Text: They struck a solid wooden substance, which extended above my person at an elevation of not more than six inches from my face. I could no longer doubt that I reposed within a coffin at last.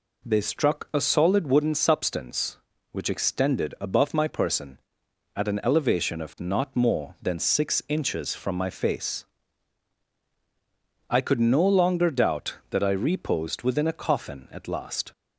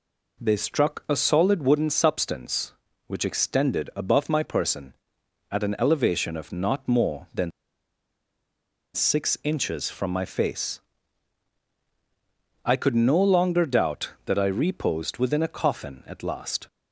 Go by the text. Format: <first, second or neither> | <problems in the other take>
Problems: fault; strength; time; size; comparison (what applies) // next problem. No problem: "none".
first | pauses between "than" and "six"; strong; at 7.4 s; 1.4 s long